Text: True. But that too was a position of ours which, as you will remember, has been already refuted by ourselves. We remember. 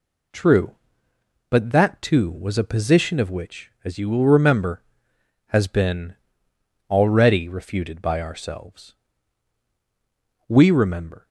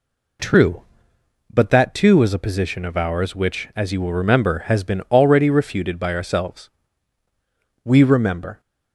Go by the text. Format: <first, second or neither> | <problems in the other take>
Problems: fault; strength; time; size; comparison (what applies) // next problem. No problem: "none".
second | skips "ours"; at 3.2 s // pauses between "been" and "already"; noticeable; at 6.1 s; 0.74 s long